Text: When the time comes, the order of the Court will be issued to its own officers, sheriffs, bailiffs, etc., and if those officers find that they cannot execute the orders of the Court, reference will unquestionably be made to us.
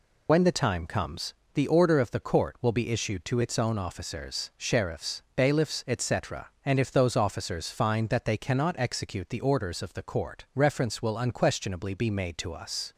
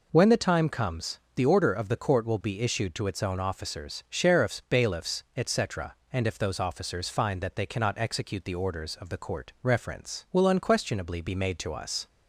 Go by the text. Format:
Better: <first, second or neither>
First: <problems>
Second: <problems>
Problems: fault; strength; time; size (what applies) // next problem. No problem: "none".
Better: second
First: loses the start of "When"; at 0.2 s; 70 ms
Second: none